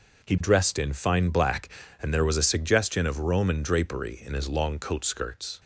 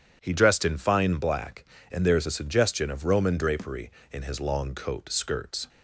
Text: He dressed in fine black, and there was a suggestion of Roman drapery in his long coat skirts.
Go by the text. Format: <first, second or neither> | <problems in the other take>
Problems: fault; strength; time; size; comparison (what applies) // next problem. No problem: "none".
first | starts louder than the rest; strong; until 1.2 s; 9 dB // says "is" for "was"; at 2.1 s